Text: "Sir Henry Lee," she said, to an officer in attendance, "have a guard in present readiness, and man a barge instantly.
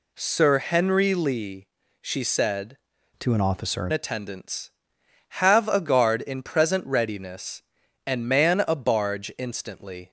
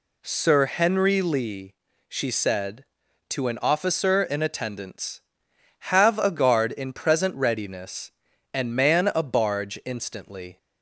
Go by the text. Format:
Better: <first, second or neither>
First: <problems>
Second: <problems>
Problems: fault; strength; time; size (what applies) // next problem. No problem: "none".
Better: second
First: changes voice from "to" to "in"; from 3.1 to 3.9 s; 0.8 s long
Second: none